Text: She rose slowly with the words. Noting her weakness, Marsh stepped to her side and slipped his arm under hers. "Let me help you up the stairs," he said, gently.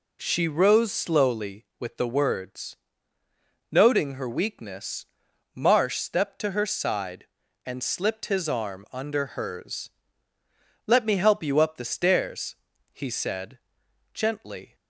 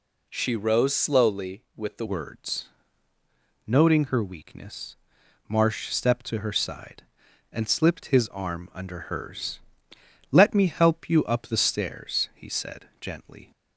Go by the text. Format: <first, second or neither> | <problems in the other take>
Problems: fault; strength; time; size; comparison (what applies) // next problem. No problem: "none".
first | changes voice at "words"; from 2.0 s on; 11.5 s long